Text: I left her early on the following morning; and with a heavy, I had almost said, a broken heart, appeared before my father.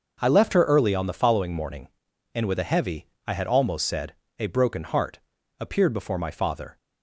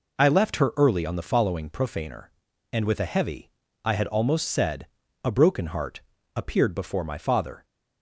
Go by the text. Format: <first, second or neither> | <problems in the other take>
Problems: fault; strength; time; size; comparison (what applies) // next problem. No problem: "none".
first | says "profaner" for "morning"; at 1.7 s